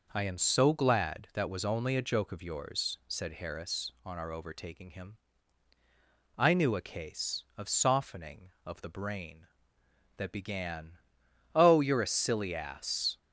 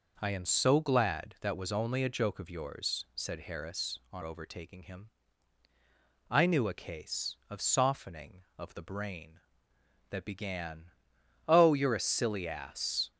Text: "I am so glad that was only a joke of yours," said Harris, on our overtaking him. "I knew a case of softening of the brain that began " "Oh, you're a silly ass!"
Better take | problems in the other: first | skips "our"; at 4.2 s

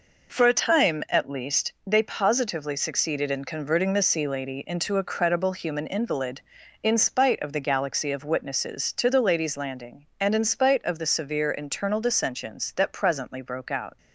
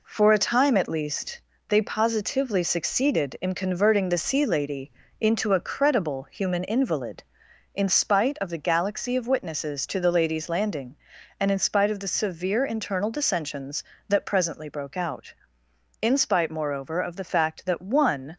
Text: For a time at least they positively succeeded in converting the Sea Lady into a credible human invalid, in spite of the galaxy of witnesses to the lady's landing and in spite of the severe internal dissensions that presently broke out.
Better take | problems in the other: first | pauses between "least" and "they"; slight; at 1.4 s; 0.26 s long // pauses between "Lady" and "into"; slight; at 4.9 s; 0.28 s long // goes on to say "In spite moreover of the fact that one"; strong; from 16.0 s on; 2.3 s long

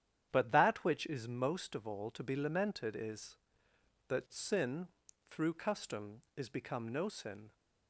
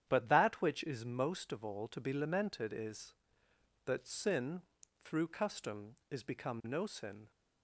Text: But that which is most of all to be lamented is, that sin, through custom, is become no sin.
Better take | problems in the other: neither | starts louder than the rest; strong; the same in both

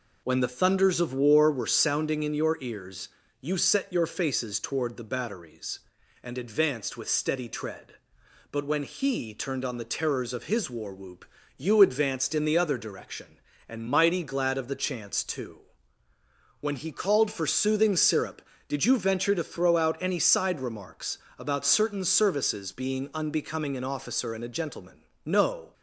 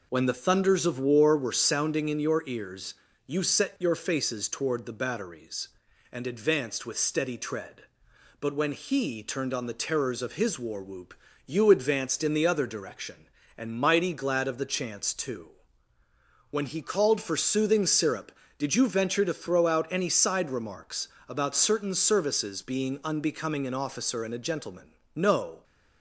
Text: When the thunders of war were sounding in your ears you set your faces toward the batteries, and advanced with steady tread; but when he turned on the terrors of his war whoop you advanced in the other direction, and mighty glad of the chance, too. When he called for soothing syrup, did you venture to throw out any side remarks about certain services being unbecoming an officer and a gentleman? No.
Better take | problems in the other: neither | pauses between "ears" and "you"; slight; the same in both // pauses between "whoop" and "you"; slight; the same in both // pauses between "remarks" and "about"; slight; the same in both

